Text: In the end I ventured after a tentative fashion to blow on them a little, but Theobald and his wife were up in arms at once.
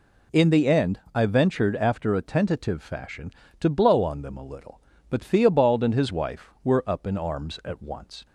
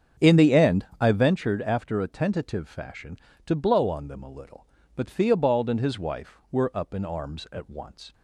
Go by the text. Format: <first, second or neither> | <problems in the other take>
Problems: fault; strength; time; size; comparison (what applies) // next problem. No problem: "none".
first | starts louder than the rest; strong; until 1.4 s; 7.5 dB // pauses between "end" and "I"; slight; at 0.8 s; 0.16 s long; slight in the first